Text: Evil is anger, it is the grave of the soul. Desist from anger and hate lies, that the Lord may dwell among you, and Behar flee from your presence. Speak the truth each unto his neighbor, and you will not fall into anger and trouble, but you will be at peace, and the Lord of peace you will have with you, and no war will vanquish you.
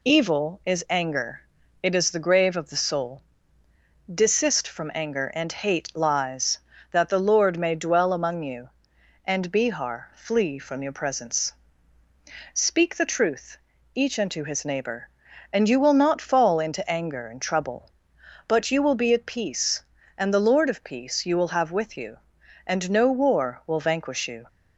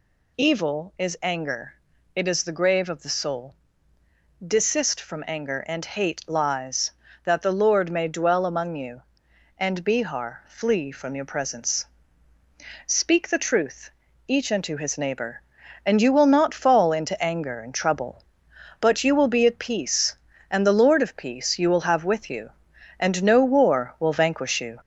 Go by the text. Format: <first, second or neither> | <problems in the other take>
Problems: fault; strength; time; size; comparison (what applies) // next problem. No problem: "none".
first | gets louder; throughout; 3.5 dB // pauses between "truth" and "each"; slight; at 13.9 s; 0.34 s long; slight in the first